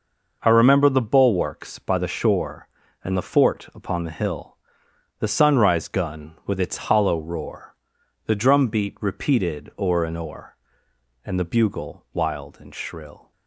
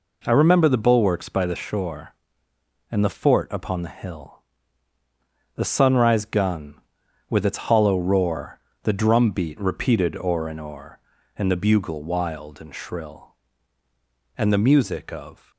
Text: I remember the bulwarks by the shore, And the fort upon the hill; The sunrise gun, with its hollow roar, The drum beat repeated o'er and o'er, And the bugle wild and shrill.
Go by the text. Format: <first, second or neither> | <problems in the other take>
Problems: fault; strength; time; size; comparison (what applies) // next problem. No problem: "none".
first | goes on to say "And the music of"; noticeable; from 14.3 s on; 1.1 s long